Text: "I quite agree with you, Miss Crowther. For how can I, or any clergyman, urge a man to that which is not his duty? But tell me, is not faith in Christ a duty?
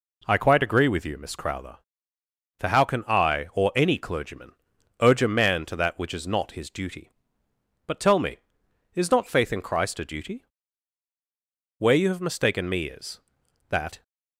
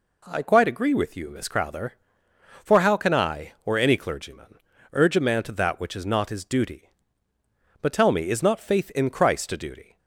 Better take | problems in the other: second | goes on to say "Where you have mistaken me is that"; strong; from 11.7 s on; 2.2 s long

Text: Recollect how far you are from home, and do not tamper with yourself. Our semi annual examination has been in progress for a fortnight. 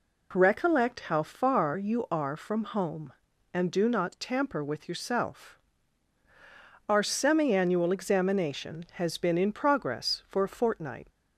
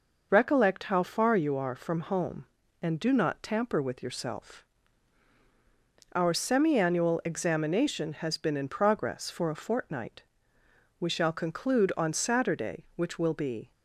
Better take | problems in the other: first | goes on to say "We shall conclude on Saturday which will be"; strong; from 10.9 s on; 2.7 s long

